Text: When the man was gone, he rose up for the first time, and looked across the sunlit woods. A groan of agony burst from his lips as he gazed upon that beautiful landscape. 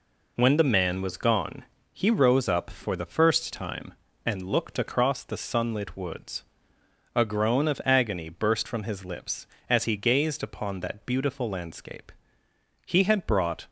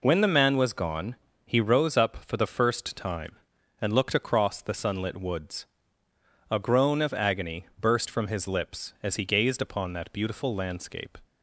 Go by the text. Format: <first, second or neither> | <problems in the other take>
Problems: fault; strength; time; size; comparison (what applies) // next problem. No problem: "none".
second | goes on to say "He had brought"; noticeable; from 12.8 s on; 0.84 s long